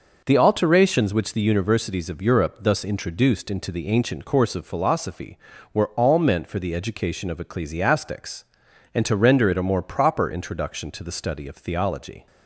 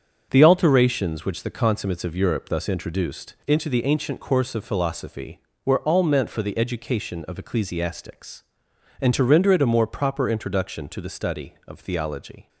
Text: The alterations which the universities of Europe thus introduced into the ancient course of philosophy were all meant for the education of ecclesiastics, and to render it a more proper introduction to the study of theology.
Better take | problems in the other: first | starts louder than the rest; until 1.3 s; 6.5 dB // says "consummates" for "universities"; at 1.4 s

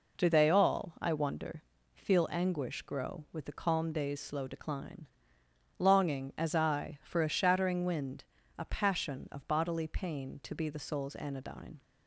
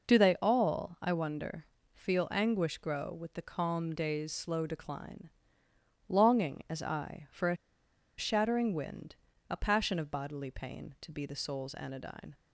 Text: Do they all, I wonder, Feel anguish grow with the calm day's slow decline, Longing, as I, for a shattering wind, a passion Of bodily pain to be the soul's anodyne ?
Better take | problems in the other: first | pauses between "a" and "shattering"; noticeable; at 7.5 s; 0.61 s long

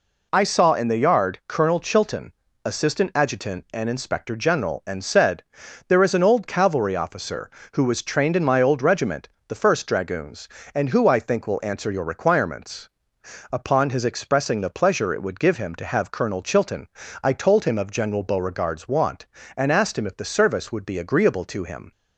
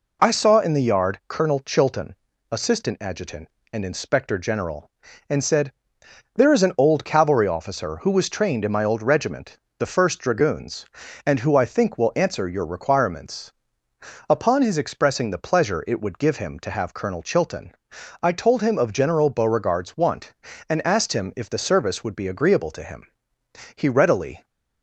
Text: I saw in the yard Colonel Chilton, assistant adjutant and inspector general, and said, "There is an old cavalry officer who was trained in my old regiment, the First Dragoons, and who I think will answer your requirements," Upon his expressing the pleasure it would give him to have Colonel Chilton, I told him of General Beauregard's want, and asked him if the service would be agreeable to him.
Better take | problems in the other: first | goes on to say "He readily"; noticeable; from 23.7 s on; 0.70 s long

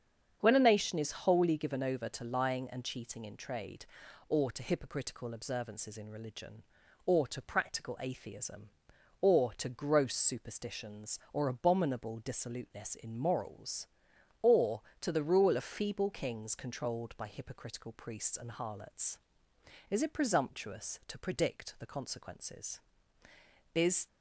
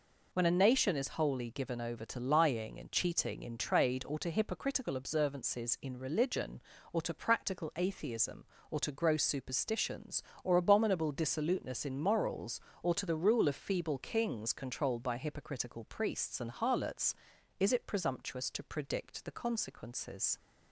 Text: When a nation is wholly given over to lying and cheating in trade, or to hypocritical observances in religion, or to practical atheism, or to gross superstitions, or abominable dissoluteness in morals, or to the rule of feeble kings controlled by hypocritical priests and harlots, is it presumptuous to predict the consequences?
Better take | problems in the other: second | starts louder than the rest; strong; until 1.4 s; 8 dB // goes on to say "Is"; slight; from 23.7 s on; 0.32 s long

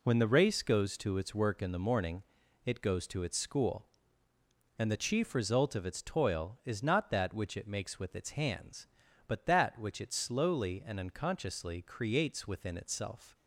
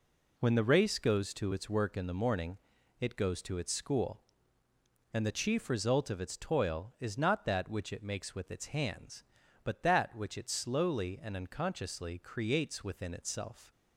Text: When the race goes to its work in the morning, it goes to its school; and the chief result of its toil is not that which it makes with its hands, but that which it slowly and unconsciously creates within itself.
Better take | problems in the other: neither | none

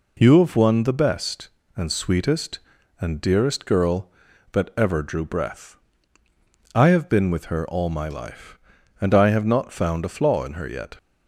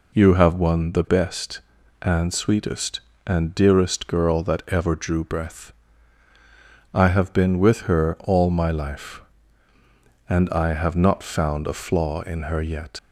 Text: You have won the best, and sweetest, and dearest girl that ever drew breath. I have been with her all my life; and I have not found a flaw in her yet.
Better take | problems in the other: first | leaves "yet" unfinished; at 12.9 s; 50 ms

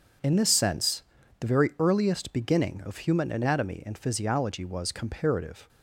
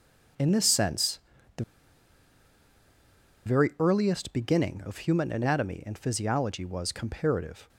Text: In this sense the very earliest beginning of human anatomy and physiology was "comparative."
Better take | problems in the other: first | pauses between "sense" and "the"; at 1.1 s; 0.38 s long; also in the first // pauses between "the" and "very"; strong; at 1.6 s; 1.8 s long

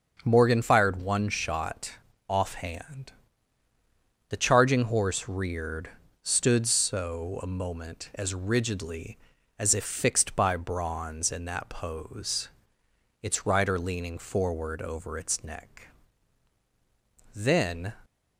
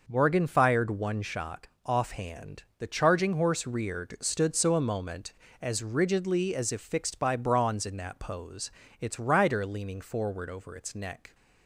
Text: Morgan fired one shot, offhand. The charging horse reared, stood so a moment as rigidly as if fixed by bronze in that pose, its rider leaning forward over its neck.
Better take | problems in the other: second | starts louder than the rest; until 1.2 s; 6.5 dB // goes on to say "Then"; from 17.3 s on; 0.58 s long

